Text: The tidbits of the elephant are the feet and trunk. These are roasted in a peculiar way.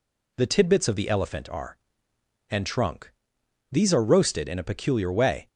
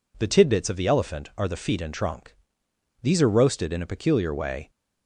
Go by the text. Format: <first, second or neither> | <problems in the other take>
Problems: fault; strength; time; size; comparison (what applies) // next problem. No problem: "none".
second | skips "the feet"; at 2.1 s